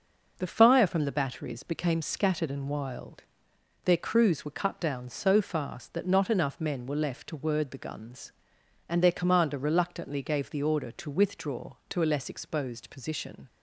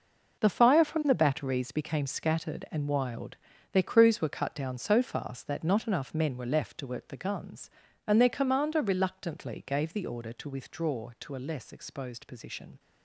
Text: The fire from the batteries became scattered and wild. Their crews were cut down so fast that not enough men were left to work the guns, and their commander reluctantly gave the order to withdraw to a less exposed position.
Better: second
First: says "word" for "work"; at 7.3 s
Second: none

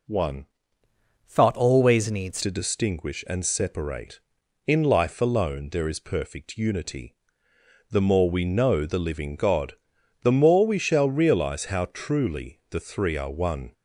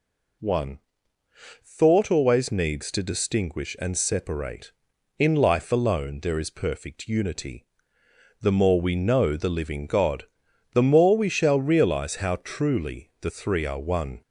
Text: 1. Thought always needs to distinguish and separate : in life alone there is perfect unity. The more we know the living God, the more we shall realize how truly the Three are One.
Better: second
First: changes voice from "Thought" to "needs"; from 1.2 to 2.4 s; 1.2 s long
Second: none

